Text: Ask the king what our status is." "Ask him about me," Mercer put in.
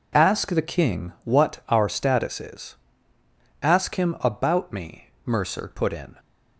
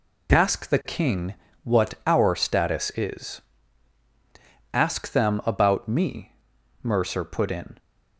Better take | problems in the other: first | pauses between "king" and "what"; slight; at 1.3 s; 0.28 s long // says "them" for "him"; at 5.1 s

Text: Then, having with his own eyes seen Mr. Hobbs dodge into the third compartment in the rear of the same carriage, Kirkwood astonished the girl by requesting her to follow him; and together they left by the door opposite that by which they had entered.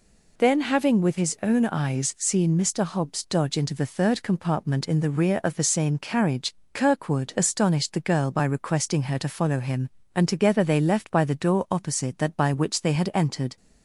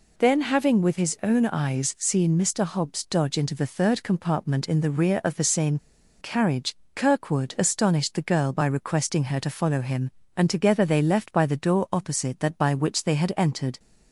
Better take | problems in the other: first | pauses between "same" and "carriage"; at 5.7 s; 0.43 s long

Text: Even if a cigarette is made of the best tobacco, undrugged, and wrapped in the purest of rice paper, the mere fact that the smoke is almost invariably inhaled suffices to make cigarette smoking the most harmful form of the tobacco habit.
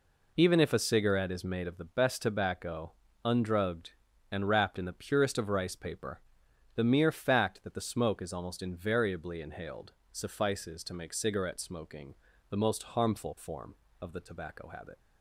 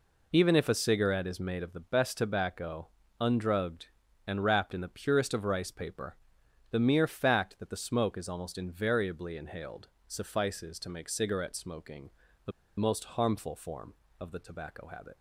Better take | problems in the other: first | pauses between "inhaled" and "suffices"; slight; at 9.8 s; 0.20 s long; slight in the first // pauses between "smoking" and "the"; slight; at 12.1 s; 0.34 s long; slight in the first // pauses between "the" and "most"; slight; at 12.5 s; 0.27 s long

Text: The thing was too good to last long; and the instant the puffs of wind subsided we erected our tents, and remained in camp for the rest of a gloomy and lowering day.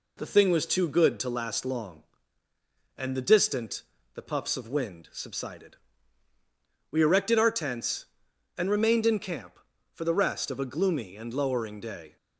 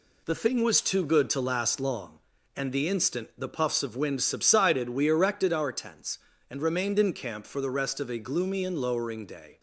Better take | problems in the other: second | says "distant" for "instant"; at 3.2 s // pauses between "subsided" and "we"; at 5.7 s; 1.1 s long

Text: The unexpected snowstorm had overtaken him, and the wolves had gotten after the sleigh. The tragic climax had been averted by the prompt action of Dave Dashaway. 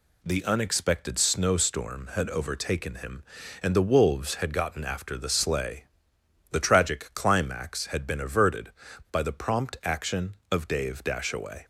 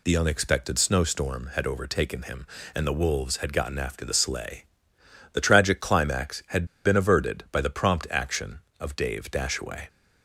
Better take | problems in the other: first | pauses between "had" and "been"; slight; at 6.6 s; 0.19 s long

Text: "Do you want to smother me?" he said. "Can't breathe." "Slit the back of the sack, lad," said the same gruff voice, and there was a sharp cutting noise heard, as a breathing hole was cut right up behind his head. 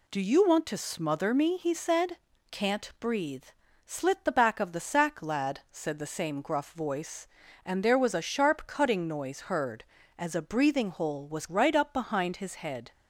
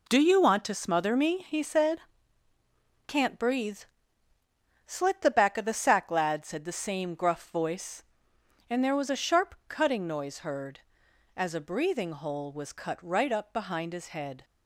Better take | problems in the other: second | skips "cut"; at 11.4 s

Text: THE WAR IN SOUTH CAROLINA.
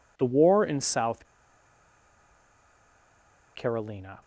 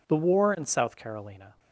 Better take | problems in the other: second | pauses between "SOUTH" and "CAROLINA"; strong; at 1.2 s; 2.2 s long

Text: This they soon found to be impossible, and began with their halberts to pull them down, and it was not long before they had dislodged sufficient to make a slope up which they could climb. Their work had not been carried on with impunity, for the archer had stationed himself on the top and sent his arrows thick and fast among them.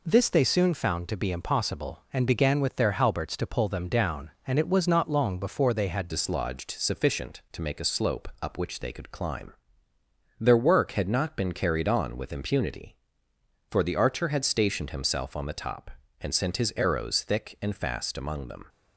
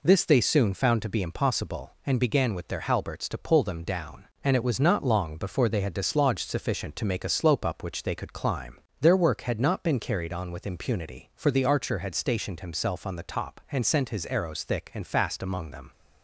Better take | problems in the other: second | changes voice at "dislodged"; from 6.0 s on; 12.6 s long

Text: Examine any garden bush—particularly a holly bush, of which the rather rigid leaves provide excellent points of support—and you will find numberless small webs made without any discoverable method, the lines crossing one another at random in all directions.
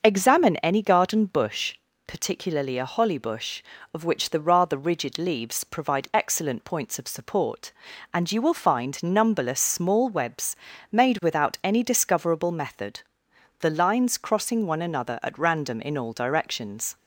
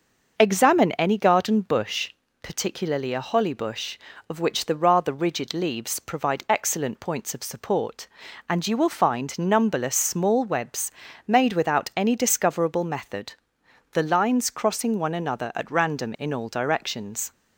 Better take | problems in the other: neither | starts louder than the rest; the same in both // pauses between "webs" and "made"; slight; the same in both

